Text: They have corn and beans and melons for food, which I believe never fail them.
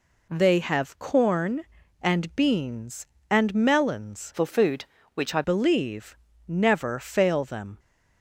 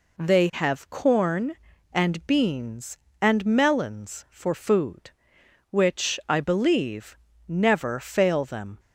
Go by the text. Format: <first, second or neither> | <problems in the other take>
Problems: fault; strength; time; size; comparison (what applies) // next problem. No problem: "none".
second | changes voice from "for" to "I"; from 4.3 to 5.4 s; 1.1 s long // pauses between "believe" and "never"; slight; at 6.1 s; 0.32 s long; slight in the second